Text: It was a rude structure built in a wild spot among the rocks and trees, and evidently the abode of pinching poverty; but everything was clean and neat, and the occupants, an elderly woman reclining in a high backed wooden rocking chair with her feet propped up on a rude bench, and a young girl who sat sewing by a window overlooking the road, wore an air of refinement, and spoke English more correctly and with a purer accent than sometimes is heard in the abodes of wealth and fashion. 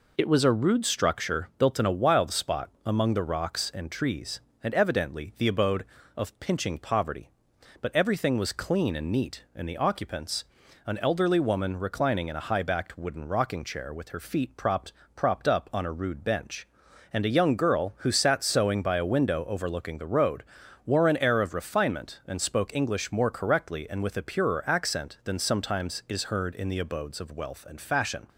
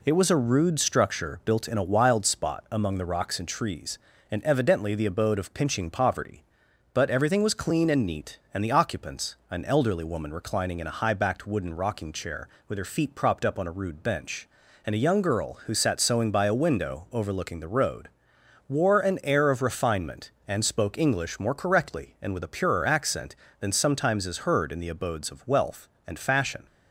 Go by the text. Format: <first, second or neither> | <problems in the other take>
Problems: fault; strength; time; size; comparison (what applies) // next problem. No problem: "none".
second | pauses between "spot" and "among"; slight; at 2.6 s; 0.16 s long // says "propped" twice; at 15.1 s